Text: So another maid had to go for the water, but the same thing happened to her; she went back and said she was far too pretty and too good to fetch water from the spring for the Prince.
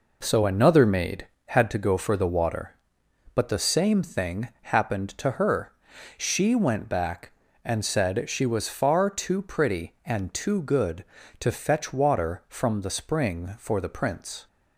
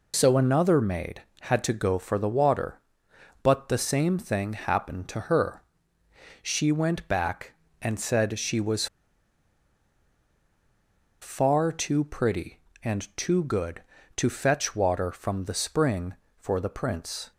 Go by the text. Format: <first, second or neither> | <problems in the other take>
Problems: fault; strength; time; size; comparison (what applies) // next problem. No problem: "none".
first | pauses between "was" and "far"; strong; at 8.8 s; 2.3 s long